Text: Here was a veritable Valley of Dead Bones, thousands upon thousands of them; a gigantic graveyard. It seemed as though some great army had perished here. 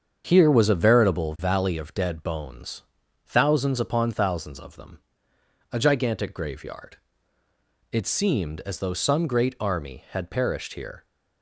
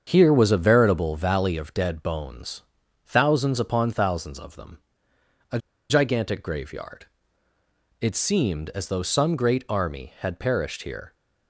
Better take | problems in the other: first | starts louder than the rest; until 1.0 s; 7 dB; also in the first // pauses between "a" and "gigantic"; slight; at 5.5 s; 0.31 s long

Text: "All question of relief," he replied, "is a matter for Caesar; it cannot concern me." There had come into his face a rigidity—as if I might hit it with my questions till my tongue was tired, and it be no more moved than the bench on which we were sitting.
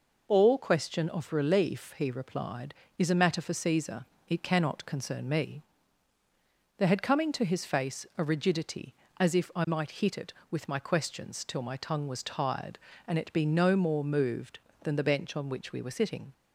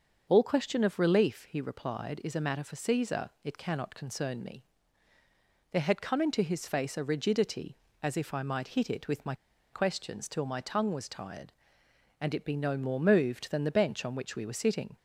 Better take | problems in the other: first | starts louder than the rest; until 1.3 s; 6.5 dB // pauses between "my" and "questions"; at 9.3 s; 0.38 s long

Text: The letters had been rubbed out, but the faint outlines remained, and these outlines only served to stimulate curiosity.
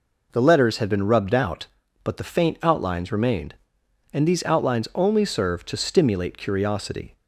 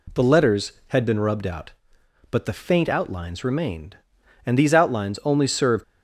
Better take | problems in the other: first | stops before "to stimulate curiosity"; at 5.8 s

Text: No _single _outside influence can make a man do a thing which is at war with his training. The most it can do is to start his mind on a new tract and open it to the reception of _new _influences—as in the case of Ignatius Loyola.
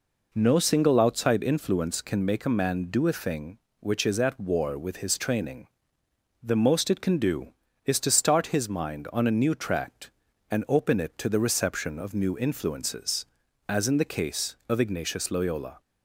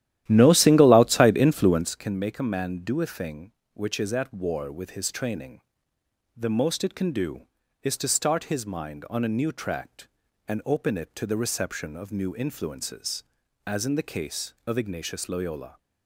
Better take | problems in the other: first | starts louder than the rest; strong; until 1.9 s; 13 dB

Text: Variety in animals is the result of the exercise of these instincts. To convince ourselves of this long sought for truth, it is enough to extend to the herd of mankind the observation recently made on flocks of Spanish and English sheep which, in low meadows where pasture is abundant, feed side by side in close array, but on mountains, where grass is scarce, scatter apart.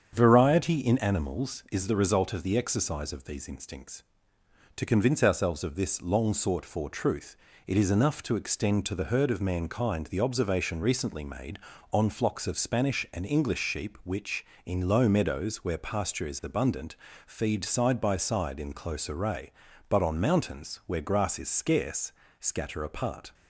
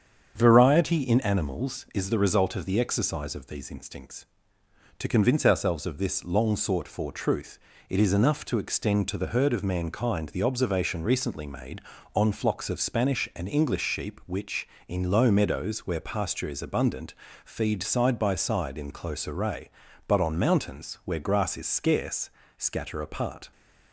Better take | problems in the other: neither | starts louder than the rest; strong; the same in both

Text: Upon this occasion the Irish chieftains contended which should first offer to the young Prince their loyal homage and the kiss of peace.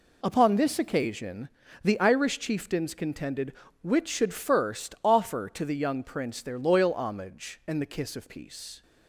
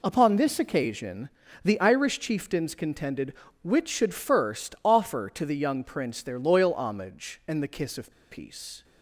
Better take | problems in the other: first | pauses between "occasion" and "the"; slight; at 1.2 s; 0.34 s long; slight in the first // pauses between "of" and "peace"; slight; at 8.1 s; 0.18 s long

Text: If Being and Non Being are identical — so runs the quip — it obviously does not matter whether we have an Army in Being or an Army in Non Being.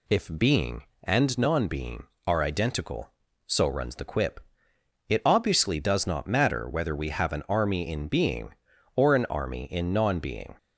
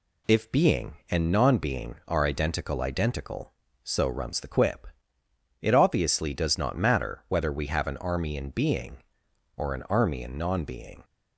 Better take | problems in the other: first | says "identical" twice; at 2.8 s

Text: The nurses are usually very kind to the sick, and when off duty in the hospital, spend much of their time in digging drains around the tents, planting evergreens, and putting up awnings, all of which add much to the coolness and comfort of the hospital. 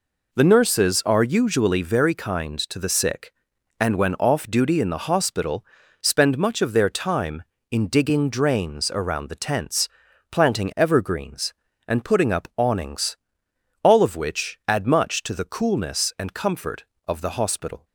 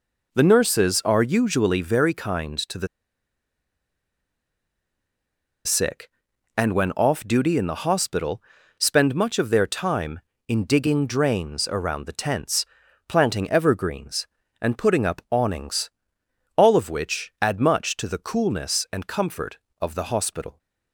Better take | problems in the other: first | pauses between "the" and "sick"; strong; at 2.8 s; 2.7 s long

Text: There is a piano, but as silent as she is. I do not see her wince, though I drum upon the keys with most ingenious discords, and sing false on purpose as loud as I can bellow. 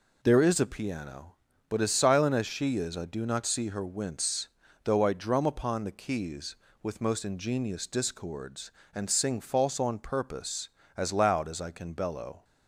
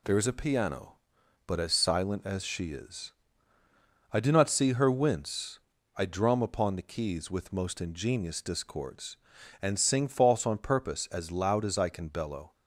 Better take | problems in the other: first | skips "though"; at 5.7 s

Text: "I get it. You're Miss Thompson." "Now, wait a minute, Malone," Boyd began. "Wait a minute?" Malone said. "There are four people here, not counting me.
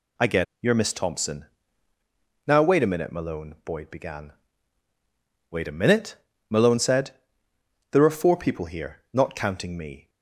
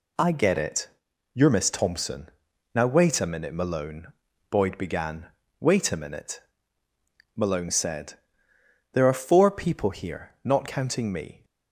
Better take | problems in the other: second | skips "it"; at 0.5 s

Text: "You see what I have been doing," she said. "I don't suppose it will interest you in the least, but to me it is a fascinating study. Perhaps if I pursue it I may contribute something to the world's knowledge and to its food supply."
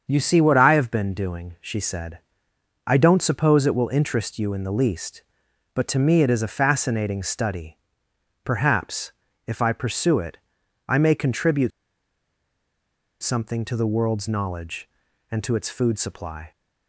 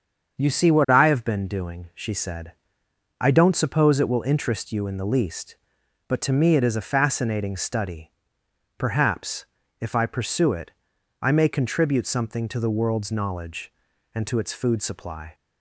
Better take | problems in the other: second | starts louder than the rest; until 1.0 s; 7 dB; also in the second // pauses between "Perhaps" and "if"; slight; at 9.1 s; 0.36 s long; slight in the second // pauses between "it" and "I"; noticeable; at 10.3 s; 0.50 s long; noticeable in the second // pauses between "contribute" and "something"; strong; at 11.7 s; 1.5 s long

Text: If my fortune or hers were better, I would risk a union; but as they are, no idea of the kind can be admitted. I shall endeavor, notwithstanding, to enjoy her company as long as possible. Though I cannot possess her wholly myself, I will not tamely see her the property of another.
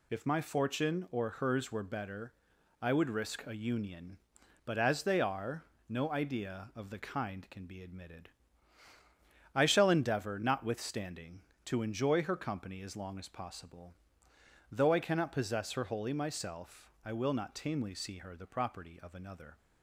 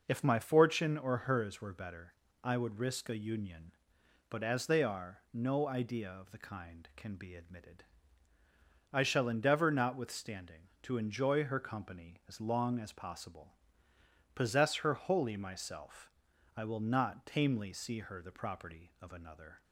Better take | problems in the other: first | skips "Though I cannot"; at 13.9 s

